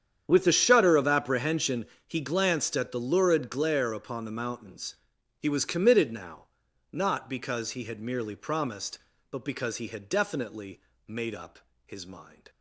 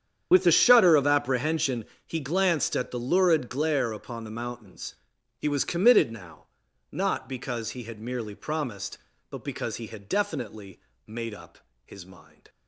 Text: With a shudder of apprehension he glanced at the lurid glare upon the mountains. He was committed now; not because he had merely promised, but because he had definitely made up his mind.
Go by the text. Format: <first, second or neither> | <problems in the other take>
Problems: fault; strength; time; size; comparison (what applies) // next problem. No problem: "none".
first | loses the start of "With"; at 0.3 s; 40 ms // starts louder than the rest; strong; until 1.3 s; 8.5 dB; strong in the first // pauses between "apprehension" and "he"; slight; at 1.8 s; 0.20 s long; slight in the first // pauses between "definitely" and "made"; slight; at 10.8 s; 0.26 s long; slight in the first // pauses between "up" and "his"; slight; at 11.5 s; 0.26 s long; slight in the first